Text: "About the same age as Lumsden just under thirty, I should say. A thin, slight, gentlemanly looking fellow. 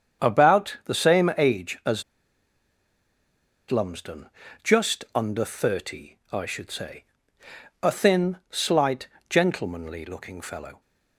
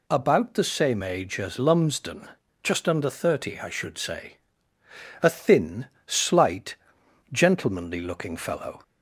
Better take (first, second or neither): second